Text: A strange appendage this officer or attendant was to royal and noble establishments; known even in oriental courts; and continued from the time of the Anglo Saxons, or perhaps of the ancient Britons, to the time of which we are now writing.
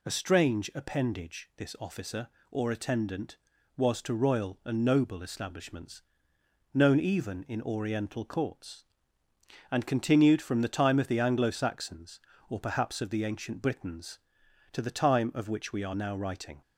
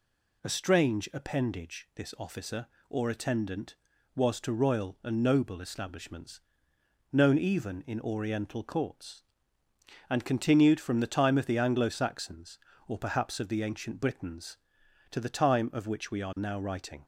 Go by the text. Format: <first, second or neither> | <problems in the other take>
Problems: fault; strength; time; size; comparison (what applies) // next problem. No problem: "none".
neither | none